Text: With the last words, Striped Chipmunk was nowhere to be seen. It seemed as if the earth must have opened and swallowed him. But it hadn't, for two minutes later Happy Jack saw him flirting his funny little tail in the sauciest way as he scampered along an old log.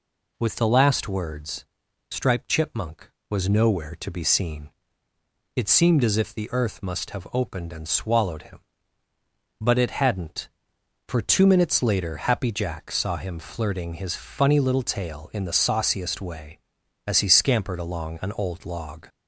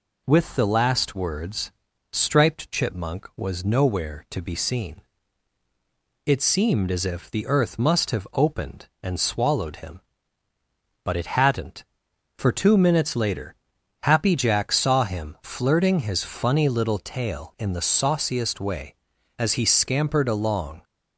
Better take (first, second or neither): first